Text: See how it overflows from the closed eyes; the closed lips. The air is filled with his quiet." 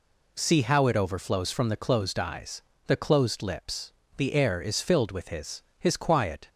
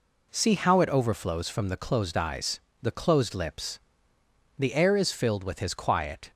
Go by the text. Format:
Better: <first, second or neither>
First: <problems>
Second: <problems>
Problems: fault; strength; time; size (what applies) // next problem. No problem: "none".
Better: second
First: says "his" twice; at 5.7 s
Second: none